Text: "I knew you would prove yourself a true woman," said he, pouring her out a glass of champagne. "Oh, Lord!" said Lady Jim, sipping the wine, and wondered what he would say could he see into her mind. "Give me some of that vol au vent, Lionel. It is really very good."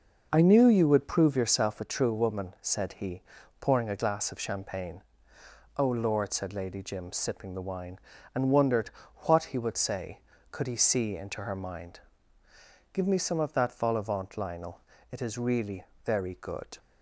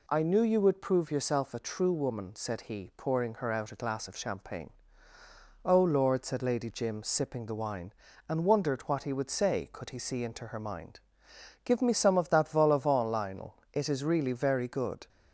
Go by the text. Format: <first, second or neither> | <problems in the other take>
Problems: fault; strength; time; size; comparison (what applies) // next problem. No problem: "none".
second | skips "her out"; at 3.8 s // pauses between "wondered" and "what"; slight; at 8.9 s; 0.34 s long // pauses between "really" and "very"; slight; at 15.8 s; 0.22 s long